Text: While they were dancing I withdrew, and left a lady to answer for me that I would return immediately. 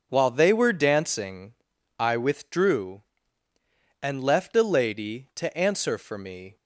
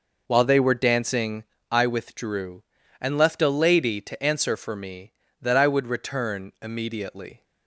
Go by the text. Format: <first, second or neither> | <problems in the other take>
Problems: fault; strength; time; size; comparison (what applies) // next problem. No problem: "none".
second | pauses between "dancing" and "I"; at 1.5 s; 0.42 s long; slight in the second // stops before "that I would return immediately"; at 6.5 s